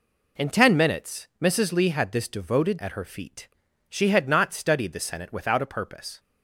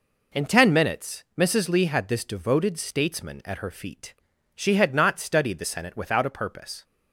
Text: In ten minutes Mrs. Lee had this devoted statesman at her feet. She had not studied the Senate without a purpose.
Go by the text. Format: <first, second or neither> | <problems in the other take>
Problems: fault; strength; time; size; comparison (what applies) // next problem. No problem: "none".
second | skips "statesman"; at 2.7 s